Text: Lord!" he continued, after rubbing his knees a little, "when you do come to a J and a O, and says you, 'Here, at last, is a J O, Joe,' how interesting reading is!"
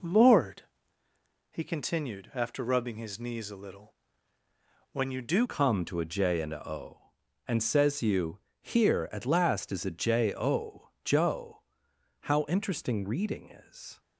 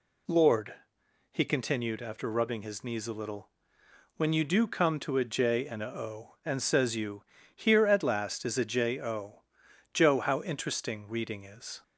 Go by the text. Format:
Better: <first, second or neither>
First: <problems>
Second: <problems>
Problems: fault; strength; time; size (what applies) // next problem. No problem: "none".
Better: second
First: changes voice at "come"; from 5.4 s on; 8.5 s long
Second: none